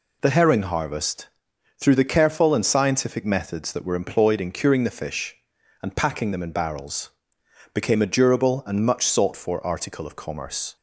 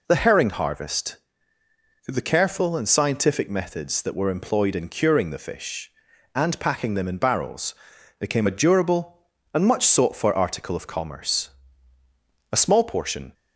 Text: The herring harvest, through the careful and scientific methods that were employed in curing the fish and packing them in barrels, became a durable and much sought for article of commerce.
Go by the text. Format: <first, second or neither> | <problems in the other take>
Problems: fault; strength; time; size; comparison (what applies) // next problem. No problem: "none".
first | goes on to say "A small portion"; noticeable; from 12.5 s on; 0.82 s long